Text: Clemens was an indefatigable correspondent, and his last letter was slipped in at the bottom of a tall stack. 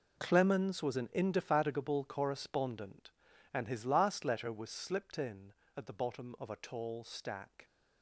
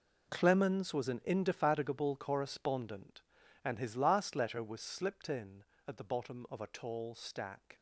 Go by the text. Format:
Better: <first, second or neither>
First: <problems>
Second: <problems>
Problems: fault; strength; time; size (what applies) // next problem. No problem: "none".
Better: neither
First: none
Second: none